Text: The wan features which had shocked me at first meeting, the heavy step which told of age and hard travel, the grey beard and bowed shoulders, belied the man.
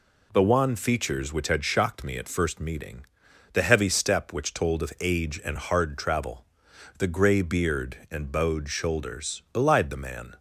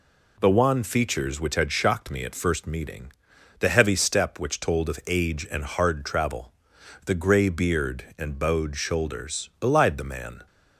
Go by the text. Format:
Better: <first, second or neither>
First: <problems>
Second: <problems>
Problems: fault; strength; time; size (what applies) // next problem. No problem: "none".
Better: neither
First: none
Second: none